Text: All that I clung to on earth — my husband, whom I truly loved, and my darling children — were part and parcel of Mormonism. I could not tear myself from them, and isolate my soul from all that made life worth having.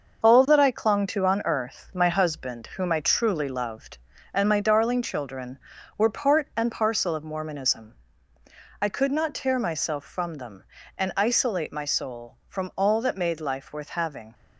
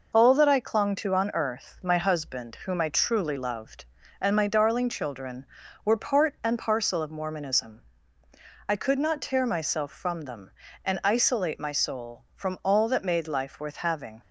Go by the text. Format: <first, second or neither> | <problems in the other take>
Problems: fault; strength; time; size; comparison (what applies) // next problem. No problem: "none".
second | gets quieter; throughout; 7 dB